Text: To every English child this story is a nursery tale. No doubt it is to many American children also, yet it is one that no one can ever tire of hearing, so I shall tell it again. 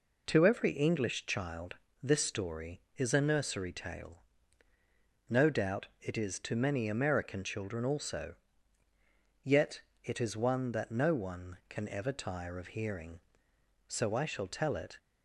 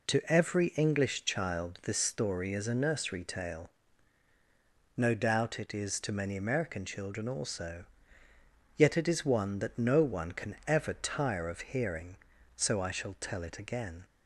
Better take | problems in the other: second | pauses between "child" and "this"; slight; at 1.7 s; 0.26 s long // pauses between "yet" and "it"; slight; at 9.8 s; 0.22 s long // stops before "again"; at 14.9 s

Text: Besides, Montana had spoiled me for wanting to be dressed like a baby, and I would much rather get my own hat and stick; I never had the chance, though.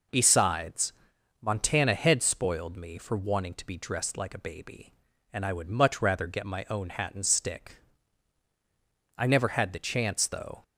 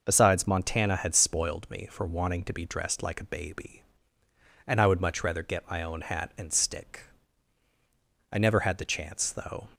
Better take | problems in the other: neither | none

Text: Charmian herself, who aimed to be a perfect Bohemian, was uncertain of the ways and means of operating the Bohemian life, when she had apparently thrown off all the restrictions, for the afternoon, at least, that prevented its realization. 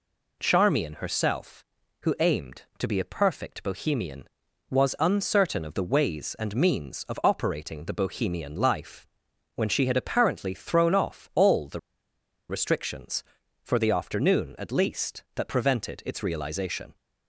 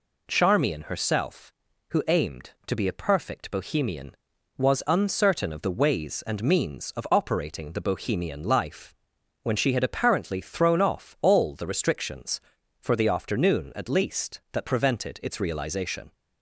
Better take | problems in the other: second | pauses between "the" and "restrictions"; noticeable; at 11.7 s; 0.70 s long

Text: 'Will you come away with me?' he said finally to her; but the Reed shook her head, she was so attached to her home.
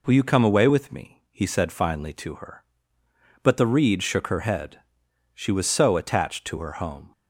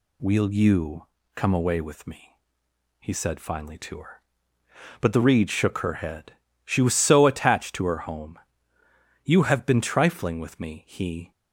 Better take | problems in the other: first | pauses between "you" and "come"; slight; at 1.0 s; 0.28 s long // goes on to say "You have been trifling with me he"; strong; from 9.2 s on; 2.0 s long

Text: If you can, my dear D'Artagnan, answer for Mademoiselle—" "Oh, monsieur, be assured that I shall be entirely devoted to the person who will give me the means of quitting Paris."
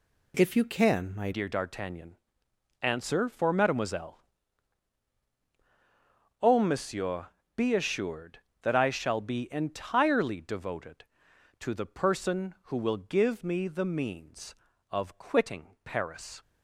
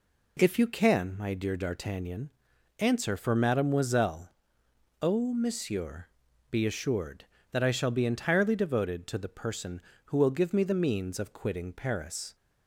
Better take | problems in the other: second | changes voice at "dear"; from 1.3 s on; 15.1 s long

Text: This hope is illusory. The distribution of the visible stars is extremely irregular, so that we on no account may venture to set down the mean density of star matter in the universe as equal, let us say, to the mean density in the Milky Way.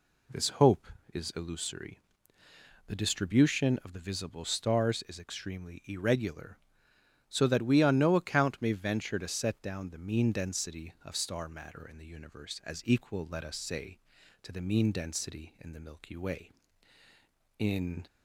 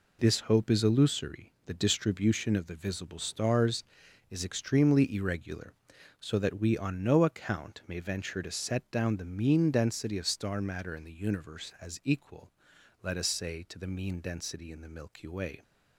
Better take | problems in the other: second | goes on to say "In"; slight; from 17.5 s on; 0.48 s long

